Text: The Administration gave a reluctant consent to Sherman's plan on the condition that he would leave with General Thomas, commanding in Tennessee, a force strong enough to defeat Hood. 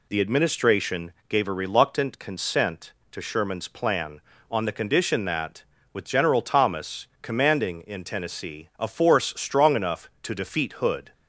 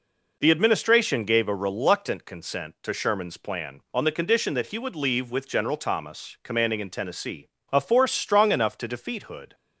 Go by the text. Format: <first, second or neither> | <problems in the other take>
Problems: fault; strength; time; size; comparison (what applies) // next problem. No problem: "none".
second | pauses between "Administration" and "gave"; slight; at 1.1 s; 0.16 s long // skips "he would leave"; at 5.7 s